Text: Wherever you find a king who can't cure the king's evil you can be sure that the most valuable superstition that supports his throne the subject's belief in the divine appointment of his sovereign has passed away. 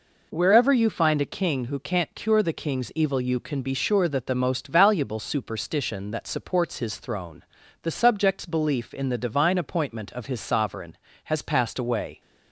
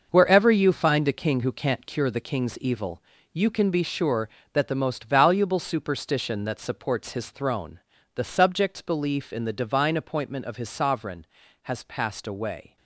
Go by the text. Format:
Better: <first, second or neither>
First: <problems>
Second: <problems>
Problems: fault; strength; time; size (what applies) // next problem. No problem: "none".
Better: first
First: pauses between "throne" and "the"; at 7.4 s; 0.40 s long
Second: gets quieter; strong; throughout; 9 dB // pauses between "evil" and "you"; slight; at 3.0 s; 0.32 s long // pauses between "throne" and "the"; at 7.7 s; 0.38 s long